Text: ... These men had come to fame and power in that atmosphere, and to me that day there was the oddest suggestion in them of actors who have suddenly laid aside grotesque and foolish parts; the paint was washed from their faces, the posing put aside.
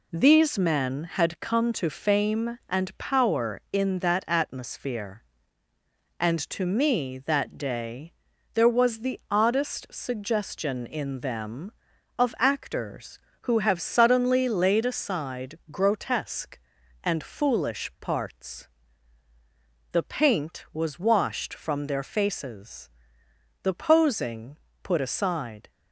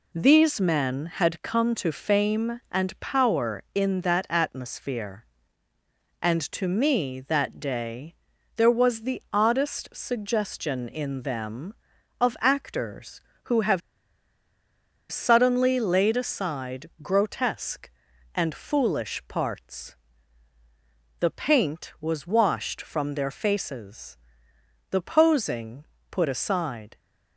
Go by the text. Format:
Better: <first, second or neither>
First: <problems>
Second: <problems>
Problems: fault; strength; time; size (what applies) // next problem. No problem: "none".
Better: first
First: pauses between "day" and "there"; at 8.1 s; 0.42 s long // pauses between "posing" and "put"; slight; at 24.5 s; 0.28 s long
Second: pauses between "day" and "there"; at 8.1 s; 0.42 s long // pauses between "have" and "suddenly"; strong; at 13.8 s; 1.3 s long // pauses between "posing" and "put"; slight; at 25.8 s; 0.28 s long